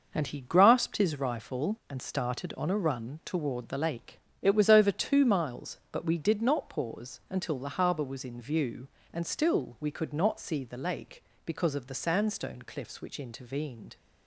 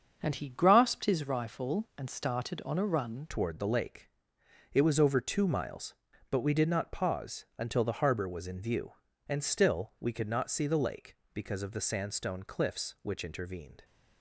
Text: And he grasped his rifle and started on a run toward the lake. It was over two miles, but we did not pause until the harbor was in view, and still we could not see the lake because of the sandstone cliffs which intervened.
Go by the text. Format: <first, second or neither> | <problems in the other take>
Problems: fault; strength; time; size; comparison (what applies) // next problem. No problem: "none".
first | starts louder than the rest; until 1.2 s; 6.5 dB // changes voice at "toward"; from 3.2 s on; 10.6 s long